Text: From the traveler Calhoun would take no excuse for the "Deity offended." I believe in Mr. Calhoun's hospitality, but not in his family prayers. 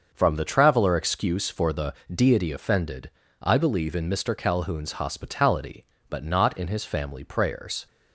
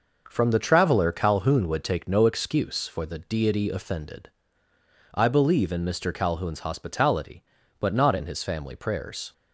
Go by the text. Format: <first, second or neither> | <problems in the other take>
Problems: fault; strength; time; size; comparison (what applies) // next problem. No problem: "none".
second | starts louder than the rest; until 1.1 s; 6.5 dB // skips "Calhoun would take no"; at 0.9 s // pauses between "the" and "Deity"; slight; at 1.9 s; 0.20 s long